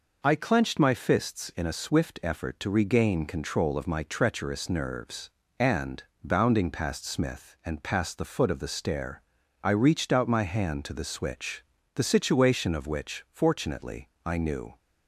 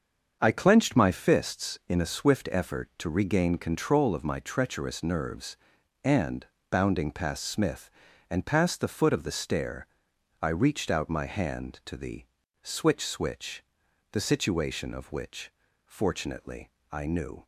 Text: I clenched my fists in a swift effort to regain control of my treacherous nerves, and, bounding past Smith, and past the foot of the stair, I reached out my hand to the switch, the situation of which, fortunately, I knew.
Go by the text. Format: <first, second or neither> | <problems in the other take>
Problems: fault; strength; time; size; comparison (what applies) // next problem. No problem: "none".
first | starts louder than the rest; until 1.4 s; 6.5 dB // pauses between "the" and "switch"; at 12.2 s; 0.38 s long // says "switch" twice; at 13.0 s